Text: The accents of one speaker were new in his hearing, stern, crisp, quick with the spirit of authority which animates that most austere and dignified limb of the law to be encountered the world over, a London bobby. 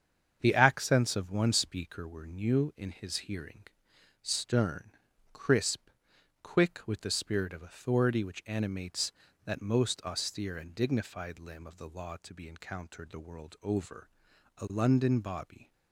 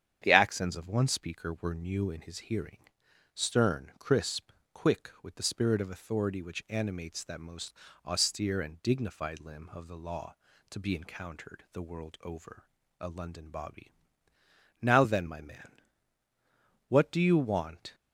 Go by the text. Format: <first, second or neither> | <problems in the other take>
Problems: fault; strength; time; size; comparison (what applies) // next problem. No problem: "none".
first | starts louder than the rest; strong; until 1.2 s; 9 dB; strong in the first // pauses between "most" and "austere"; slight; at 7.7 s; 0.34 s long // goes on to say "Now then my man what do you want"; strong; from 14.8 s on; 3.1 s long